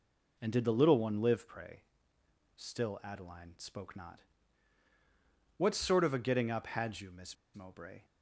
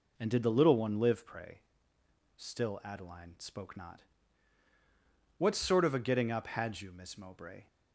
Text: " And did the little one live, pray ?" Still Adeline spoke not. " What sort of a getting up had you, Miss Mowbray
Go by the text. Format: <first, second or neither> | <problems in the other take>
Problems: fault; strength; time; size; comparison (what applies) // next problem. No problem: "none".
second | pauses between "Miss" and "Mowbray"; slight; at 7.3 s; 0.19 s long